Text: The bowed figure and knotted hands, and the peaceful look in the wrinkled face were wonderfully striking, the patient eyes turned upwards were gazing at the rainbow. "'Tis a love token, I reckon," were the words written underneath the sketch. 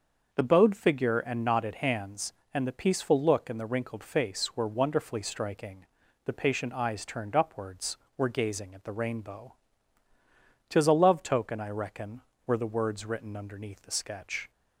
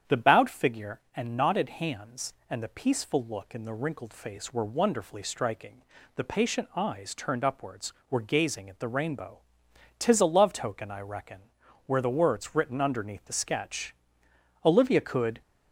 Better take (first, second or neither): first